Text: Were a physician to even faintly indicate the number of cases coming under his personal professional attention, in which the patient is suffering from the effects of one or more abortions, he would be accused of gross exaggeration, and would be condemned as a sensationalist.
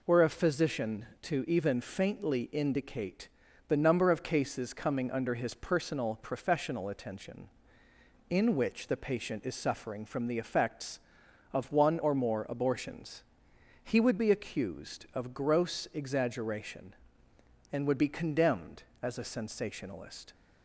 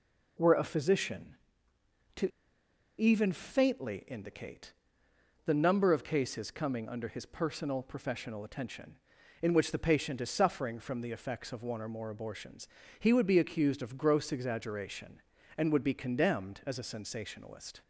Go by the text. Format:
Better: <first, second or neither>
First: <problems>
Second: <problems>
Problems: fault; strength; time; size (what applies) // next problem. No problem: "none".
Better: first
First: pauses between "indicate" and "the"; at 3.2 s; 0.40 s long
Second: pauses between "to" and "even"; noticeable; at 2.3 s; 0.69 s long // pauses between "indicate" and "the"; noticeable; at 4.7 s; 0.72 s long